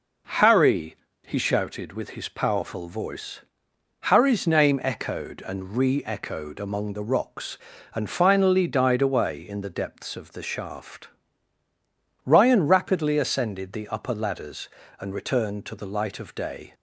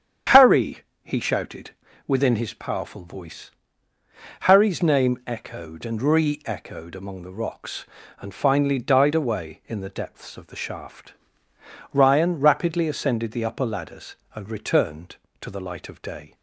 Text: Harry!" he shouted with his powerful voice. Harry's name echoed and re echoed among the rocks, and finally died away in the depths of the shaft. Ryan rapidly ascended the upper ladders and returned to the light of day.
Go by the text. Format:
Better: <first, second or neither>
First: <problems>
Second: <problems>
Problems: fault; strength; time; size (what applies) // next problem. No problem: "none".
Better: first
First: none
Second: starts louder than the rest; strong; until 1.5 s; 8.5 dB // says "within" for "with"; at 2.0 s